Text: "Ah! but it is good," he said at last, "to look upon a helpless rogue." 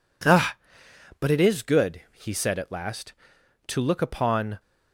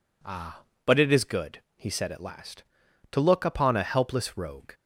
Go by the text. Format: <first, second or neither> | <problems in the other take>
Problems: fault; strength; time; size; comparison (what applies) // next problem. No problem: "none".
second | stops before "a helpless rogue"; at 4.6 s